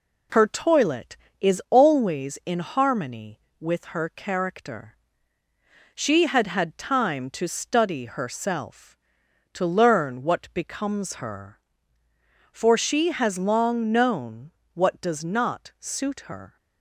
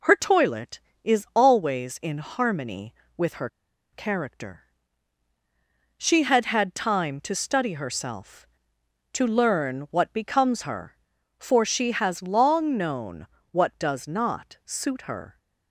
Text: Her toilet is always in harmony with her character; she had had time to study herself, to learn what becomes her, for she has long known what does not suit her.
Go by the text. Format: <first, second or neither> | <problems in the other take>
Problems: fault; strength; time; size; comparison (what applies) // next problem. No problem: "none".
first | pauses between "her" and "character"; at 3.4 s; 0.43 s long // pauses between "known" and "what"; slight; at 13.2 s; 0.26 s long; slight in the first